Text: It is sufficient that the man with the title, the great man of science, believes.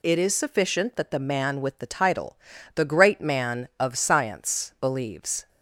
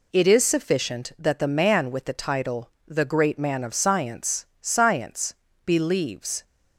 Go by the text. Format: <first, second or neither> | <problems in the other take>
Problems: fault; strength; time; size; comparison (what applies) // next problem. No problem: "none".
first | says "science" twice; at 4.6 s